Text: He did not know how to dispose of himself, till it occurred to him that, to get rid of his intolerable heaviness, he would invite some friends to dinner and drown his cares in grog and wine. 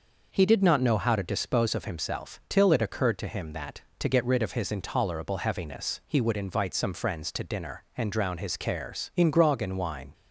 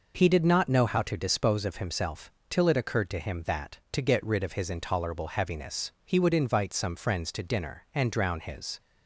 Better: first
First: none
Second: stops before "cares in grog and wine"; at 8.7 s

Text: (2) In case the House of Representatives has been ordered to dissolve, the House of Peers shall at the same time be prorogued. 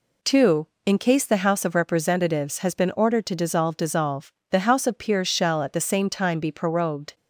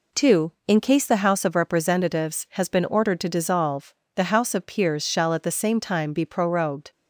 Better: second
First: says "dissolve" twice; at 3.7 s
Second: none

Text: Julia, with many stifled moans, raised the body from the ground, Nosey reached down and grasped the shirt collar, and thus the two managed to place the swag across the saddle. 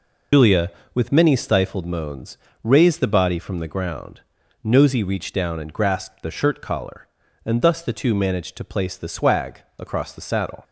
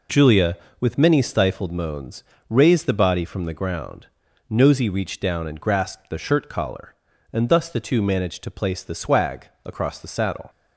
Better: second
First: loses the start of "Julia"; at 0.3 s; 90 ms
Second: none

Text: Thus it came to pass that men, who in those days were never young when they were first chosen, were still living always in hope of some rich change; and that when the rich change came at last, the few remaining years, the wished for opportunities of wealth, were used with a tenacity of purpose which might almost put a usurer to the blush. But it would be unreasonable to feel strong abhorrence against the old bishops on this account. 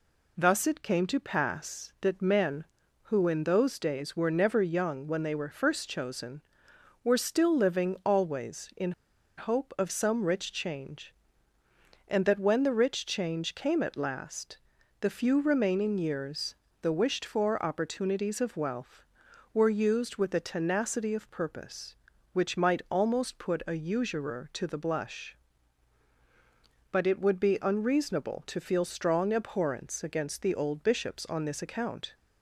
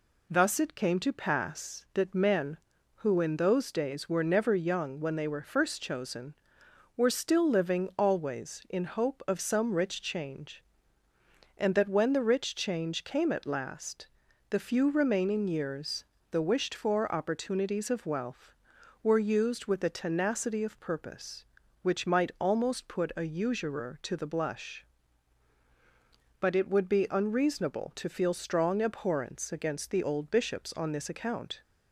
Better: second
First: pauses between "in" and "hope"; noticeable; at 8.9 s; 0.46 s long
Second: none

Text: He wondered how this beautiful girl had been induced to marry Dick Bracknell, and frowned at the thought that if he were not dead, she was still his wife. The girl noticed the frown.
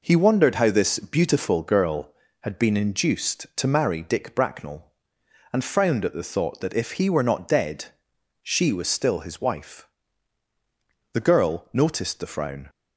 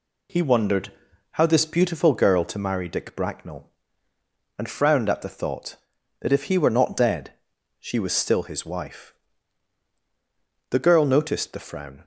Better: first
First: none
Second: pauses between "wondered" and "how"; at 0.9 s; 0.38 s long // skips "had been induced"; at 2.4 s

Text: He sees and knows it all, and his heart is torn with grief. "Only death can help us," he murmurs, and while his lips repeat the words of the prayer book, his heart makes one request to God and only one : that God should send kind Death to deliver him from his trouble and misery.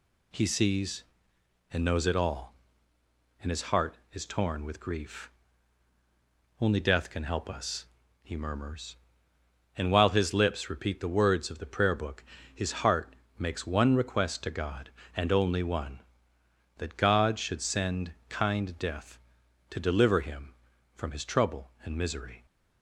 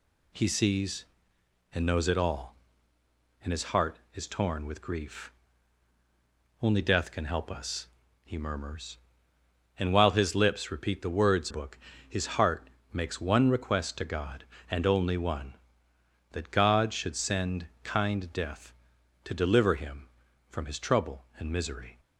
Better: first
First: pauses between "heart" and "makes"; slight; at 13.1 s; 0.24 s long // pauses between "send" and "kind"; slight; at 18.1 s; 0.16 s long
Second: skips "of the prayer"; at 11.5 s // pauses between "heart" and "makes"; slight; at 12.6 s; 0.24 s long // pauses between "send" and "kind"; slight; at 17.6 s; 0.16 s long

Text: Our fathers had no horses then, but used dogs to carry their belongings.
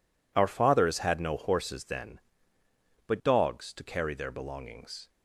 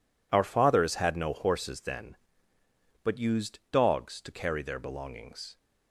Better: second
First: skips "used"; at 3.2 s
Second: none

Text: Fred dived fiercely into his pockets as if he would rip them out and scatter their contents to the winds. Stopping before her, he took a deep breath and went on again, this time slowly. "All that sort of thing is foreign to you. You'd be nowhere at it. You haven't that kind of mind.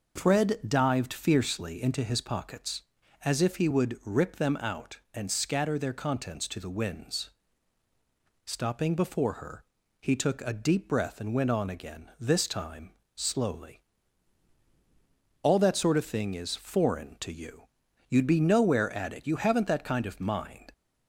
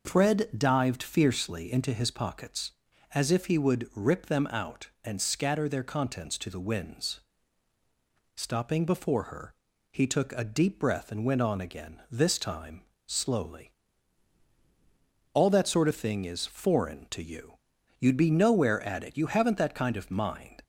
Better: neither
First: pauses between "time" and "slowly"; slight; at 12.9 s; 0.24 s long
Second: pauses between "time" and "slowly"; slight; at 12.8 s; 0.24 s long

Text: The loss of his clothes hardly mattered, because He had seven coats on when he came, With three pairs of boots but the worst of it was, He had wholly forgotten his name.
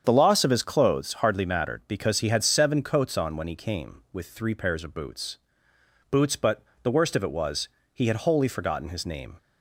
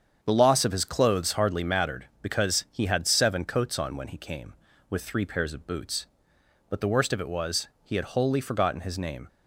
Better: second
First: starts louder than the rest; strong; until 1.0 s; 7.5 dB // says "boots" twice; at 6.1 s // pauses between "but" and "the"; slight; at 6.6 s; 0.20 s long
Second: starts louder than the rest; strong; until 1.2 s; 7.5 dB

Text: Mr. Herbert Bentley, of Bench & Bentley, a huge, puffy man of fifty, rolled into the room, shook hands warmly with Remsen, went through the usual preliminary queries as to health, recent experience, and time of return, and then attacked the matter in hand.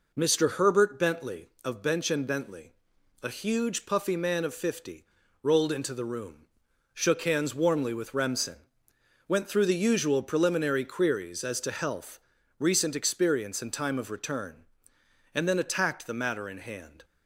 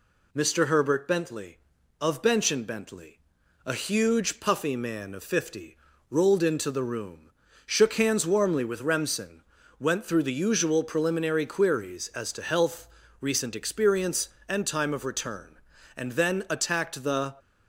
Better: first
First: none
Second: stops before "matter in hand"; at 17.3 s

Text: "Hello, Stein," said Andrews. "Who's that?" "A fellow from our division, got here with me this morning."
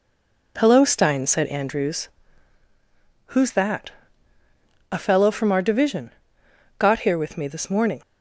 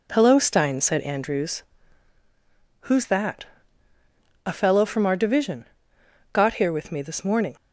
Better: second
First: stays silent before the first word; slight; until 0.5 s; 0.5 s long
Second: none

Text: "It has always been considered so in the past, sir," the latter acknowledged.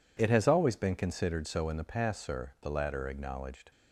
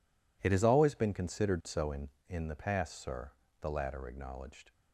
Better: first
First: none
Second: says "in" twice; at 2.2 s

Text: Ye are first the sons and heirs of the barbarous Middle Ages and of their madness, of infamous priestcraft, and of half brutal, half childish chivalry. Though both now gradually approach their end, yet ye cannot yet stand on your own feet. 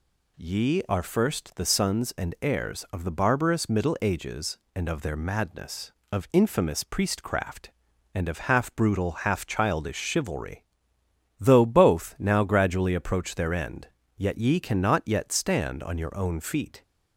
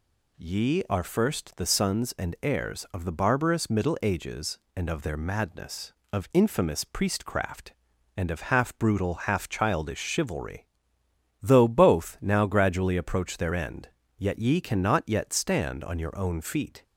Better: neither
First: none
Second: none

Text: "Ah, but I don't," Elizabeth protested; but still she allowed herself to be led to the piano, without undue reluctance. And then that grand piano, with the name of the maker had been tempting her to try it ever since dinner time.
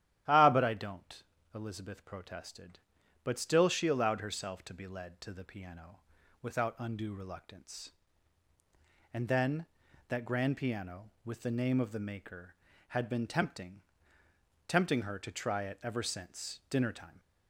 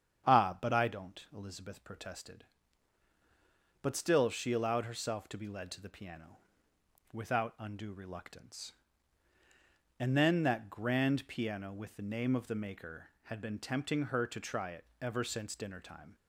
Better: second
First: starts louder than the rest; strong; until 1.5 s; 11.5 dB // says "tempting" twice; at 14.6 s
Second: starts louder than the rest; strong; until 1.3 s; 8 dB

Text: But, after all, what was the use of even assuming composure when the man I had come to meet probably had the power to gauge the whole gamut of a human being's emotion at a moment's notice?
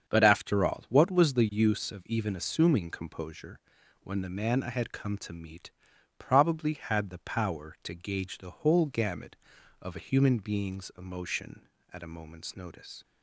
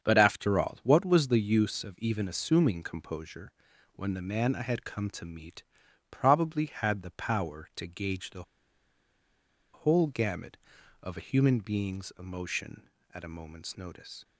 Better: first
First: starts louder than the rest; strong; until 1.1 s; 7.5 dB // pauses between "composure" and "when"; at 3.5 s; 0.42 s long // pauses between "meet" and "probably"; noticeable; at 5.7 s; 0.46 s long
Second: starts louder than the rest; strong; until 1.0 s; 7.5 dB // pauses between "composure" and "when"; at 3.5 s; 0.42 s long // pauses between "meet" and "probably"; noticeable; at 5.6 s; 0.46 s long // pauses between "the" and "whole"; strong; at 8.4 s; 1.3 s long

